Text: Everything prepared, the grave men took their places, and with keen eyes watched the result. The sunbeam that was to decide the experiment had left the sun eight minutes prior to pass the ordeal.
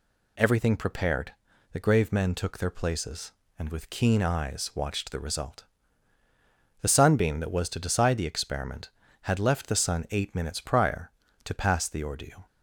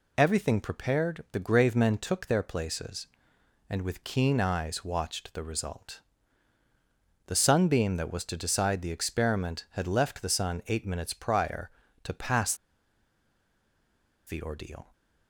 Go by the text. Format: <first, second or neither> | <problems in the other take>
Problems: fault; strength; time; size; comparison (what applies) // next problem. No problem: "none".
first | pauses between "pass" and "the"; strong; at 12.5 s; 1.7 s long